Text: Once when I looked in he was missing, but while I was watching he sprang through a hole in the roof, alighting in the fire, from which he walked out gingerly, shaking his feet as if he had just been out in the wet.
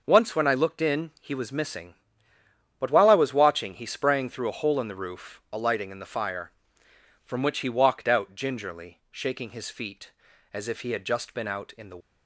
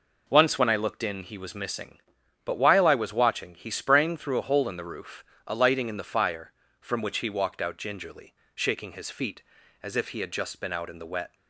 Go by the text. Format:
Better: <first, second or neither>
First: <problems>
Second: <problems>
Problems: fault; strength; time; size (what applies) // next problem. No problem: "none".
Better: second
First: stops before "wet"; at 12.0 s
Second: none